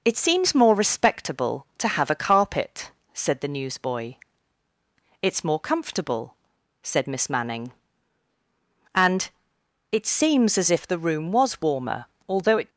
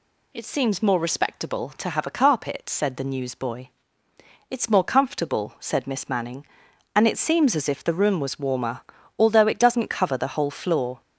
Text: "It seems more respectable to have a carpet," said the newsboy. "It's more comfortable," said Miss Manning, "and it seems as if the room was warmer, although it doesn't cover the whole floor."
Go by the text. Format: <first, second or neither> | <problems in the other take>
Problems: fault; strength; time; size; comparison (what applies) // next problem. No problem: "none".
second | pauses between "and" and "it"; noticeable; at 9.2 s; 0.62 s long // stops before "doesn't cover the whole floor"; at 12.6 s